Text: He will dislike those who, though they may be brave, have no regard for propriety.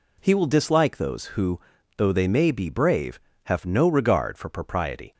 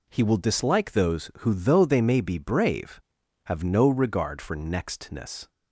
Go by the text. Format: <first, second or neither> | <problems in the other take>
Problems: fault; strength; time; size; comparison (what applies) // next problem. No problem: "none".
first | says "nextness" for "propriety"; at 4.5 s